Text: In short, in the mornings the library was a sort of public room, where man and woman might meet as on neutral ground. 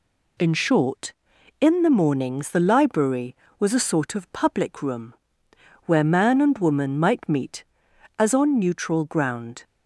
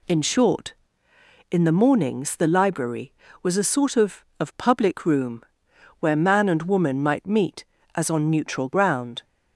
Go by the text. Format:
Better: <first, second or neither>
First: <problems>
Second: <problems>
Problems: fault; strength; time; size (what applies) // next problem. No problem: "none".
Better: first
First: none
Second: says "of" twice; at 4.3 s